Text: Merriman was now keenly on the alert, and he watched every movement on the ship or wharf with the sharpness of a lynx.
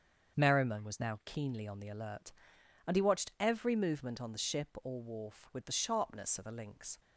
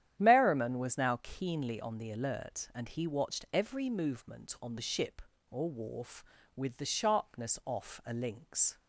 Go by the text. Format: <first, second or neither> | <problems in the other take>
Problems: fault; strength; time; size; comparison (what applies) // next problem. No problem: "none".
first | starts louder than the rest; strong; until 1.1 s; 10.5 dB; also in the first // says "off" for "of"; at 7.6 s